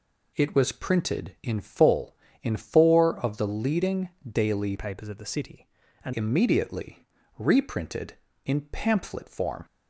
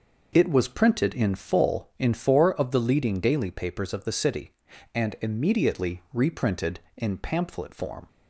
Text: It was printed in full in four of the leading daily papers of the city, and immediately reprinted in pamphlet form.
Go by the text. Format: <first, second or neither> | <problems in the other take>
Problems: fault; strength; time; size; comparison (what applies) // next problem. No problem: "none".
second | pauses between "leading" and "daily"; slight; at 4.0 s; 0.20 s long // changes voice from "papers" to "and"; from 4.7 to 6.1 s; 1.4 s long // pauses between "immediately" and "reprinted"; slight; at 7.0 s; 0.32 s long